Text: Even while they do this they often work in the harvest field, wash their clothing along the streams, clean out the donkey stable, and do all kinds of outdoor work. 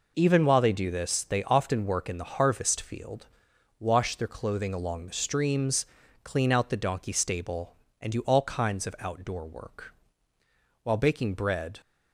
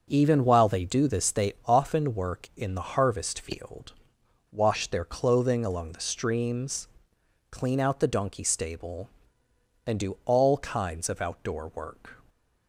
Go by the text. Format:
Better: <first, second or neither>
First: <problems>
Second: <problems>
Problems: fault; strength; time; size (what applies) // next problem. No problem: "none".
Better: second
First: goes on to say "While baking bread"; noticeable; from 10.8 s on; 0.96 s long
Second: none